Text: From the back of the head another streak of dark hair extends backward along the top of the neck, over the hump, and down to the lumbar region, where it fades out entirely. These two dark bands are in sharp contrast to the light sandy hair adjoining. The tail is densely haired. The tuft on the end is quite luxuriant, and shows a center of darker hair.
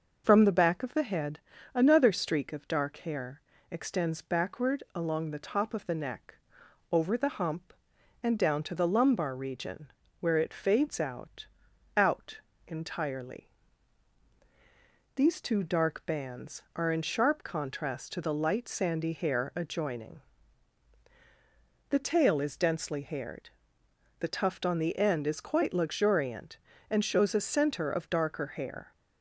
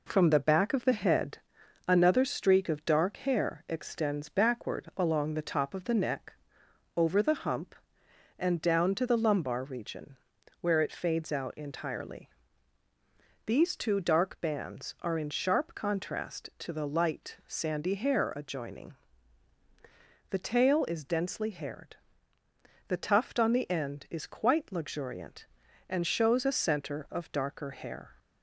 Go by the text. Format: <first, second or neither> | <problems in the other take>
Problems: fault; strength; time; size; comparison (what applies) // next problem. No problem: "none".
second | pauses between "head" and "another"; at 1.3 s; 0.38 s long; noticeable in the second // pauses between "hair" and "extends"; slight; at 3.4 s; 0.28 s long // says "out" twice; at 11.9 s